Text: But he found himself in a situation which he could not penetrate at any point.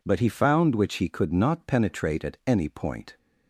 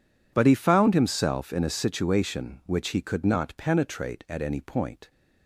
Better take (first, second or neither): second